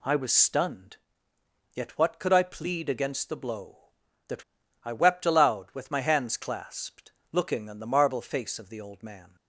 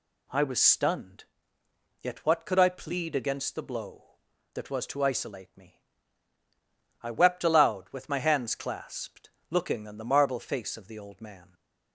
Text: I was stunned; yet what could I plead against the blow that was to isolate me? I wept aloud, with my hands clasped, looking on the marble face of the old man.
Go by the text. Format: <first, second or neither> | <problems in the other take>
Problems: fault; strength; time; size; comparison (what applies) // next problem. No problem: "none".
second | skips "was to isolate me"; at 4.6 s